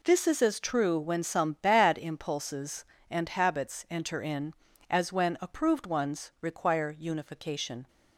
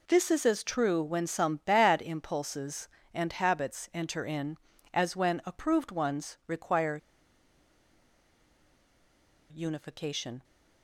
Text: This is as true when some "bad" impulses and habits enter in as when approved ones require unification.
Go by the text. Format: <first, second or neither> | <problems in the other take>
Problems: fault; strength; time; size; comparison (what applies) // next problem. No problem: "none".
first | pauses between "require" and "unification"; strong; at 6.9 s; 2.5 s long